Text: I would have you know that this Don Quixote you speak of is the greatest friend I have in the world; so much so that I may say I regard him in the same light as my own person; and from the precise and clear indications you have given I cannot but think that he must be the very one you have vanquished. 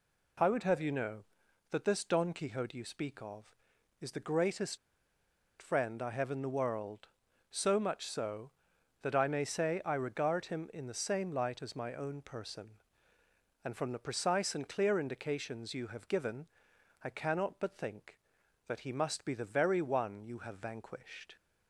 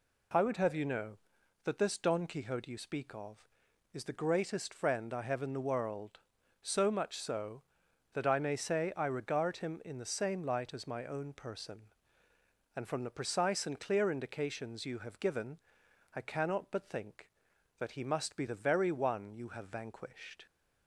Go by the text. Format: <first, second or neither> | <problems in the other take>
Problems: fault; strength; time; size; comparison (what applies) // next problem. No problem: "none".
second | pauses between "greatest" and "friend"; noticeable; at 4.7 s; 0.83 s long // pauses between "given" and "I"; noticeable; at 16.4 s; 0.56 s long; noticeable in the second